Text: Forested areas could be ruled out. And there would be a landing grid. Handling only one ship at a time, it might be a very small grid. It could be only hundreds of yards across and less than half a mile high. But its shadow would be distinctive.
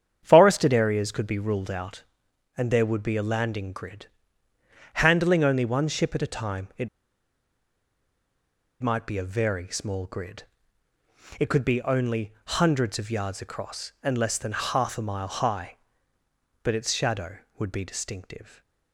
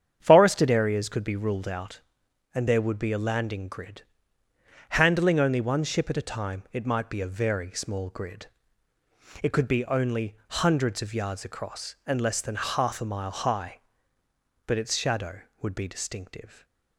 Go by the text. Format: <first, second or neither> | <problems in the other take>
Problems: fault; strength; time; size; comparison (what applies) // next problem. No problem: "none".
second | starts louder than the rest; strong; until 1.2 s; 8 dB; strong in the second // pauses between "it" and "might"; strong; at 6.8 s; 1.9 s long // stays silent after the last word; slight; from 18.4 s on; 0.5 s long; slight in the second